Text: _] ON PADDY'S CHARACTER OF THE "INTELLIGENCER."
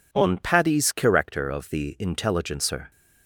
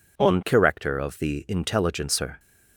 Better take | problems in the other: first | skips "PADDY'S"; at 0.4 s

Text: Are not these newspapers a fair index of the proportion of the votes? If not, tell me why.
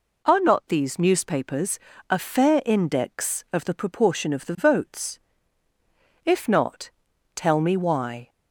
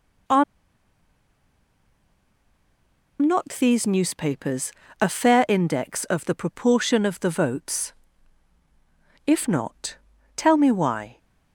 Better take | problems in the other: first | pauses between "Are" and "not"; strong; at 0.4 s; 2.7 s long // pauses between "newspapers" and "a"; slight; at 4.6 s; 0.30 s long; slight in the first

